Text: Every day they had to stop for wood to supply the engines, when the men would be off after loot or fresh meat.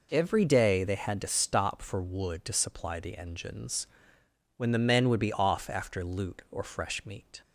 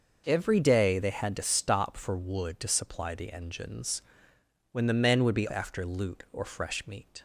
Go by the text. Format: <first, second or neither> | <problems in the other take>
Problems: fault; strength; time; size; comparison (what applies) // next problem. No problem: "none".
first | skips "off"; at 5.4 s